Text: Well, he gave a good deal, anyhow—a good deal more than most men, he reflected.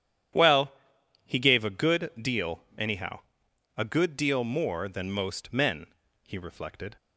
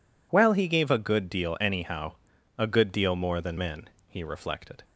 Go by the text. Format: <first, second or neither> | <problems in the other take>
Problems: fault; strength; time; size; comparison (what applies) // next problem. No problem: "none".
first | skips "most"; at 3.5 s